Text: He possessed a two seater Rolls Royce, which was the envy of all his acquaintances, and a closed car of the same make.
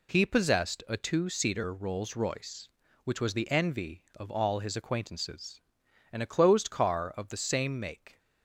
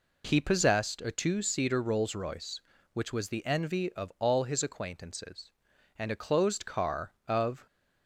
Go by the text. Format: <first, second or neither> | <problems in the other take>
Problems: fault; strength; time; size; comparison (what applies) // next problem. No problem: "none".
first | stops before "the same make"; at 7.6 s